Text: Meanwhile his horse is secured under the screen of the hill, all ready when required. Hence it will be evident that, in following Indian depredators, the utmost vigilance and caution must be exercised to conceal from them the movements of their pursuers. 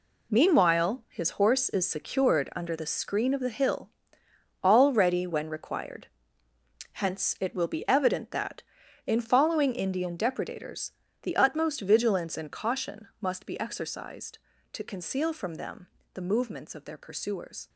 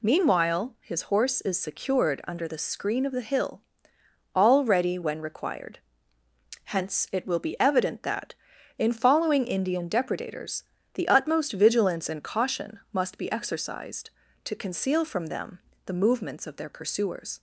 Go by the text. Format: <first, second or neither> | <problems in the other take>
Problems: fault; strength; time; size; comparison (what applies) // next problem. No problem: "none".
second | gets quieter; strong; throughout; 10 dB // pauses between "them" and "the"; slight; at 15.8 s; 0.26 s long; slight in the second